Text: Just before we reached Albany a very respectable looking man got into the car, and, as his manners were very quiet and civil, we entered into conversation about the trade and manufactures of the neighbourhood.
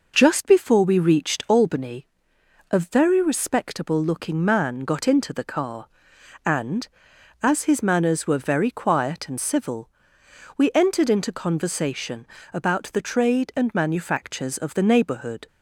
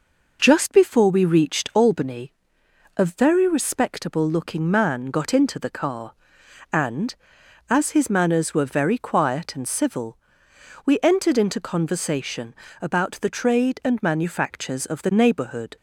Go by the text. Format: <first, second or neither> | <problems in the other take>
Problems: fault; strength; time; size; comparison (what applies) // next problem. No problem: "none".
neither | pauses between "Albany" and "a"; noticeable; the same in both // pauses between "conversation" and "about"; slight; the same in both